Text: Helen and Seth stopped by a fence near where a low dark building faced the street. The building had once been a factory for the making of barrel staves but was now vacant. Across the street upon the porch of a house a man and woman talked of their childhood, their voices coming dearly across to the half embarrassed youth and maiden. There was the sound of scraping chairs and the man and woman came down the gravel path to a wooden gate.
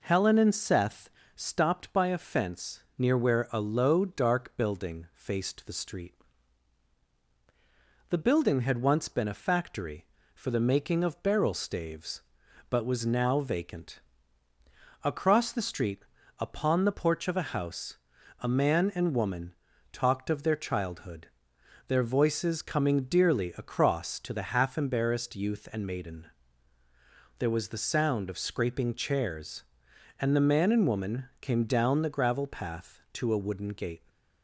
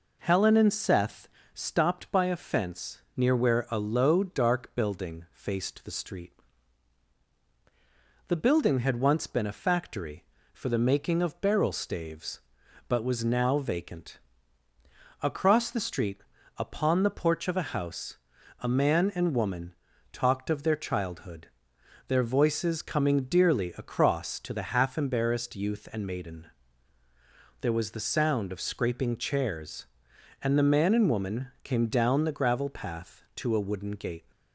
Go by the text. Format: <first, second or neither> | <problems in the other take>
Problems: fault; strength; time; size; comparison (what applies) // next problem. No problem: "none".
neither | pauses between "Seth" and "stopped"; slight; the same in both // pauses between "fence" and "near"; slight; the same in both // pauses between "street" and "upon"; the same in both // pauses between "house" and "a"; the same in both // pauses between "woman" and "talked"; the same in both